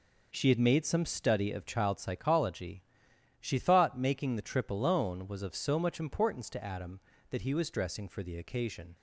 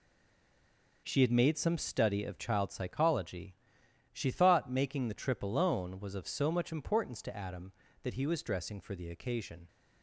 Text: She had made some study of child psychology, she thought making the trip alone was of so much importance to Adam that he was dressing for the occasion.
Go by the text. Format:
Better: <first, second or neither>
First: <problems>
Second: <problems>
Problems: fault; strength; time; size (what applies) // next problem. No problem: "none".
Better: first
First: none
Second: stays silent before the first word; until 1.0 s; 1.0 s long